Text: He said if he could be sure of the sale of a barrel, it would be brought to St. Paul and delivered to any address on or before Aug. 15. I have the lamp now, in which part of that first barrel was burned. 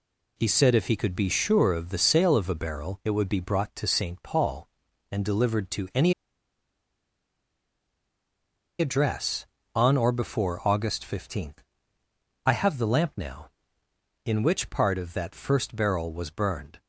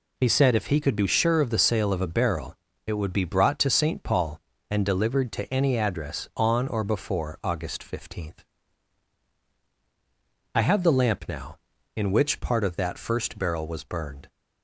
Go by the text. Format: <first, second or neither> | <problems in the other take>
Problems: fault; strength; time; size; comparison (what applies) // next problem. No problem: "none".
second | pauses between "any" and "address"; strong; at 6.1 s; 2.6 s long